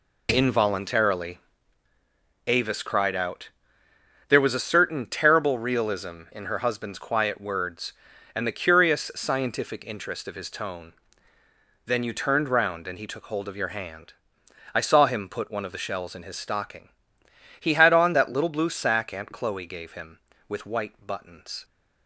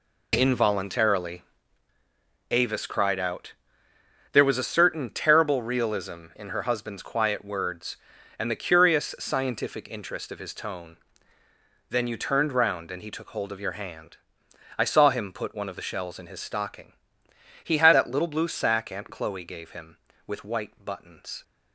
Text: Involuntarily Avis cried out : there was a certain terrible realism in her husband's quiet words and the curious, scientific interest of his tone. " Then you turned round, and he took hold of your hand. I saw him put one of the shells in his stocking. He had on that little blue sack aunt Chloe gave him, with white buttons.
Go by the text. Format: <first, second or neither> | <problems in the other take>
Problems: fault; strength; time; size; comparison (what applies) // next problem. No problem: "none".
first | pauses between "Involuntarily" and "Avis"; at 1.4 s; 1.0 s long; also in the first // skips "on"; at 17.9 s